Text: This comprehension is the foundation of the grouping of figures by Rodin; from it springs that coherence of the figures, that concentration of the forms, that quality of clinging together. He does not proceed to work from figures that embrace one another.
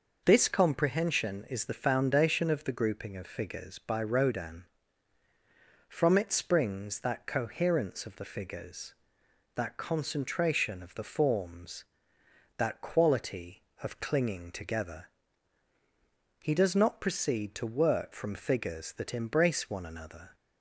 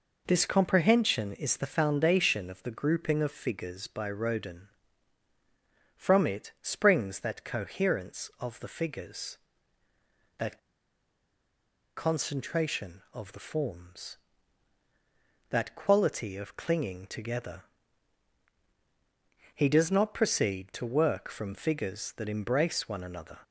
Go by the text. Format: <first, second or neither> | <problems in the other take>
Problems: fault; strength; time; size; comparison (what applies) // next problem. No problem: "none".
first | pauses between "that" and "concentration"; strong; at 10.5 s; 1.3 s long